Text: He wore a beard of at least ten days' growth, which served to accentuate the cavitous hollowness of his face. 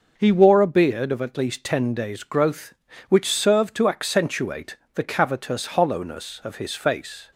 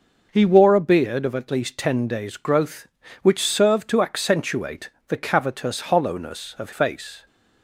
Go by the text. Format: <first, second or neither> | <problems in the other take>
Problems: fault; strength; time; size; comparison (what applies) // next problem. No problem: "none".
first | pauses between "accentuate" and "the"; slight; at 4.8 s; 0.18 s long; slight in the first // skips "his"; at 6.7 s